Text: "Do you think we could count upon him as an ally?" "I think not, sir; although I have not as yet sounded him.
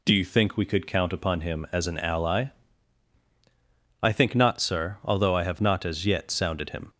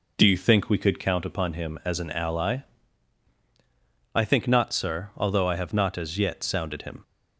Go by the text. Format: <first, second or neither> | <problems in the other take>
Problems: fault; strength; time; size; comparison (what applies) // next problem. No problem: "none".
first | starts louder than the rest; noticeable; until 1.2 s; 5 dB